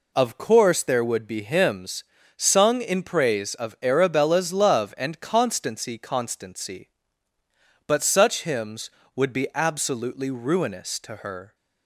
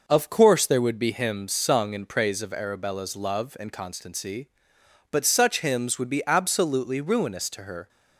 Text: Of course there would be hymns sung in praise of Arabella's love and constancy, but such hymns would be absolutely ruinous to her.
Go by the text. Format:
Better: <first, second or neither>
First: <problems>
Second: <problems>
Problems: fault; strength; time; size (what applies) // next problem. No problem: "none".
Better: second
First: pauses between "hymns" and "sung"; slight; at 2.0 s; 0.34 s long // says "constancy" twice; at 5.9 s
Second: none